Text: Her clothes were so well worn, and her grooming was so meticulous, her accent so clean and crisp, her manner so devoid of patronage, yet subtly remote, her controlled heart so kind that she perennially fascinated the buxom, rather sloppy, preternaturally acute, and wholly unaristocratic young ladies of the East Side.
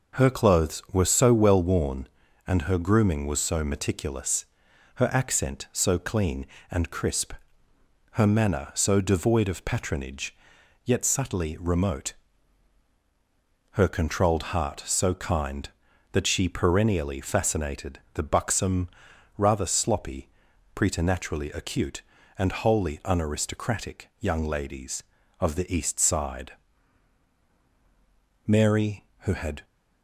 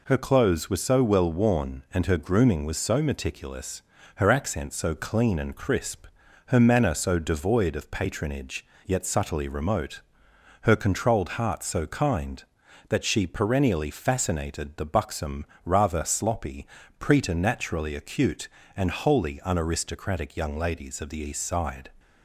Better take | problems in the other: second | goes on to say "Mary who had"; noticeable; from 28.4 s on; 1.1 s long

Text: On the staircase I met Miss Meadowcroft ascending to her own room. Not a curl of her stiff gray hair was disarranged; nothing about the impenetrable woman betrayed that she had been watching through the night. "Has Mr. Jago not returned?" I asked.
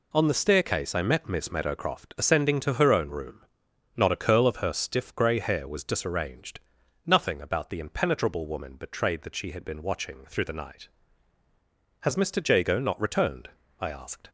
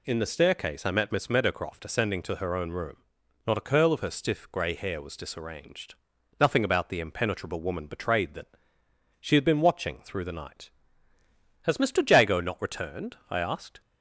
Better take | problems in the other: first | says "In" for "On"; at 0.0 s // pauses between "that" and "she"; noticeable; at 8.4 s; 0.70 s long

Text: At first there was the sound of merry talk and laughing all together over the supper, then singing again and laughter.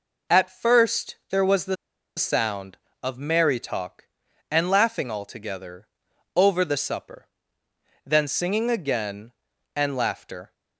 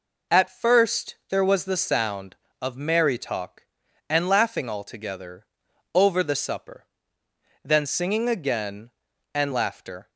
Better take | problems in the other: second | pauses between "the" and "sound"; at 1.7 s; 0.43 s long // pauses between "together" and "over"; noticeable; at 5.8 s; 0.48 s long; noticeable in the second

